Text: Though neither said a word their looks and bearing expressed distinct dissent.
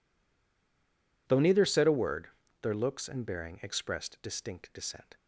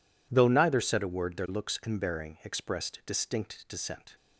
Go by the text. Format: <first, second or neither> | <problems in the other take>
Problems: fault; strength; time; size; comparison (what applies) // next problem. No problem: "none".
second | stays silent before the first word; noticeable; until 1.2 s; 1.2 s long // pauses between "word" and "their"; slight; at 2.2 s; 0.32 s long